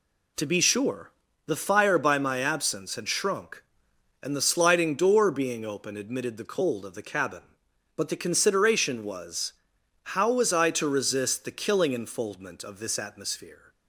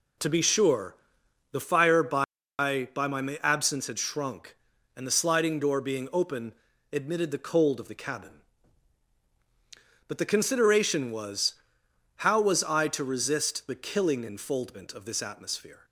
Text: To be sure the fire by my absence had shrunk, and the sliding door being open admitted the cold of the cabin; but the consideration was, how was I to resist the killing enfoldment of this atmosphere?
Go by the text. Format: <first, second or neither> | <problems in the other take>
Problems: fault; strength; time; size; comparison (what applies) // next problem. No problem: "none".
first | pauses between "sure" and "the"; noticeable; at 0.9 s; 0.56 s long; slight in the first // says "by" twice; at 2.5 s // pauses between "open" and "admitted"; at 6.5 s; 0.38 s long